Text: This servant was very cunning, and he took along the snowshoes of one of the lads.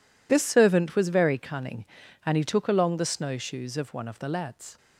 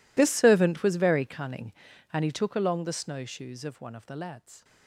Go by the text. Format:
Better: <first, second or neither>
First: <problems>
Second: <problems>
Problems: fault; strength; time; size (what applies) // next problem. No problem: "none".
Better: first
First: none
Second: gets quieter; strong; throughout; 21.5 dB